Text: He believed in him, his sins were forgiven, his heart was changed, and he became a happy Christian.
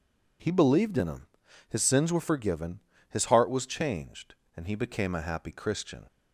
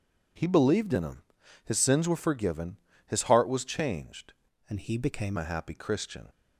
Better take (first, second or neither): first